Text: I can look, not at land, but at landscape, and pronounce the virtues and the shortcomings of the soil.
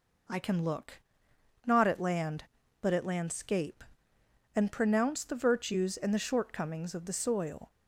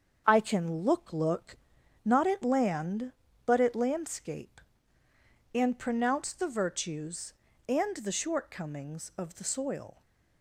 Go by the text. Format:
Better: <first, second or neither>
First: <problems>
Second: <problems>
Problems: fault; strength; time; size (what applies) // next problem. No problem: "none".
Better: first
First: none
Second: starts louder than the rest; until 1.2 s; 7 dB // says "look" twice; at 1.1 s